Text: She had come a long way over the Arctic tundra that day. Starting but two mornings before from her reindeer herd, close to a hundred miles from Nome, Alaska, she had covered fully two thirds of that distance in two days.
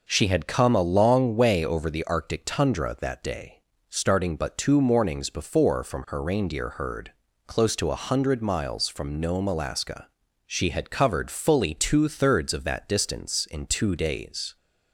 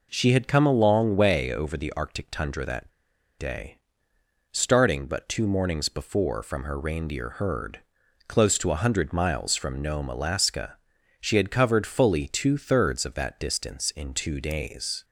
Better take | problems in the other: first | pauses between "that" and "day"; noticeable; at 2.8 s; 0.48 s long

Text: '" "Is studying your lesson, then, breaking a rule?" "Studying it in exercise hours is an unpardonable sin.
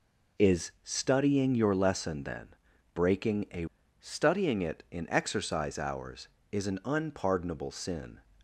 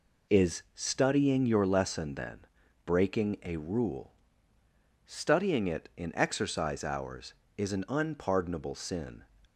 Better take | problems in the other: second | skips "rule"; at 3.8 s

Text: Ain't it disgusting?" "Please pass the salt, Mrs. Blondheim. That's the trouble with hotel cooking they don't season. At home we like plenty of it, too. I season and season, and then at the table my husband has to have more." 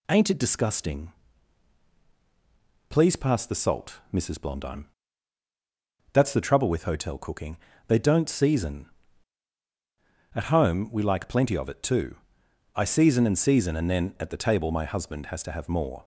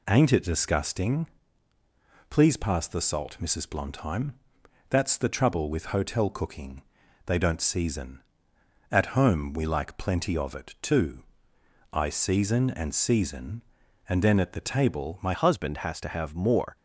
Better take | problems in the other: first | pauses between "cooking" and "they"; at 6.8 s; 0.42 s long; slight in the first // changes voice at "husband"; from 15.3 s on; 1.4 s long

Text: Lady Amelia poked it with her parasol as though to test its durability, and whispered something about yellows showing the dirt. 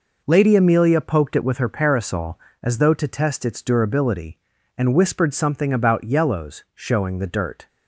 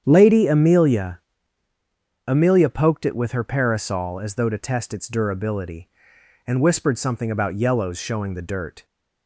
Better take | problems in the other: first | starts louder than the rest; strong; until 1.0 s; 8.5 dB // says "Amelia" twice; at 2.2 s

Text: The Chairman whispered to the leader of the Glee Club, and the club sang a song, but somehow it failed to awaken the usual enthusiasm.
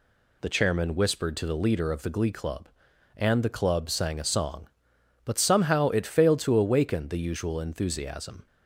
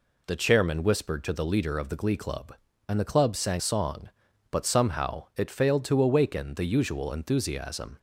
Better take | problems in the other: first | skips "a"; at 3.5 s

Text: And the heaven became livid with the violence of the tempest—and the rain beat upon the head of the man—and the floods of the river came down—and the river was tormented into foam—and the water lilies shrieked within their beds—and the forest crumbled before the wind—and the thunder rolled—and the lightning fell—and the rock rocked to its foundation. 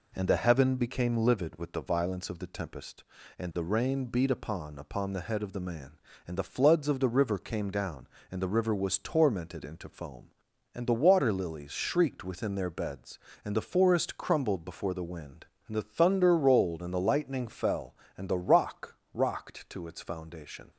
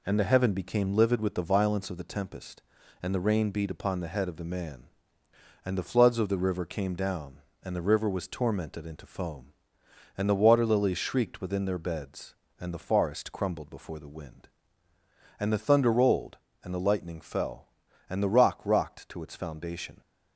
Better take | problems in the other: second | says "upon" twice; at 4.7 s // pauses between "rock" and "rocked"; slight; at 18.9 s; 0.16 s long

